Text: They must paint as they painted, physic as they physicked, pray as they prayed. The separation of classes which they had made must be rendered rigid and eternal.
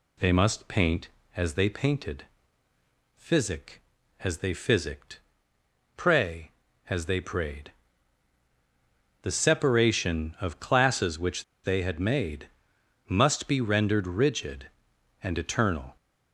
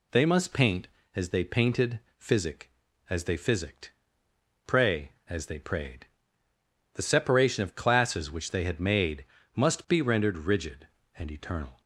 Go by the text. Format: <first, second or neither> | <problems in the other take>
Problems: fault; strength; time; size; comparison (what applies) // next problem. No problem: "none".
second | pauses between "which" and "they"; slight; at 11.4 s; 0.19 s long // pauses between "made" and "must"; noticeable; at 12.4 s; 0.60 s long; slight in the second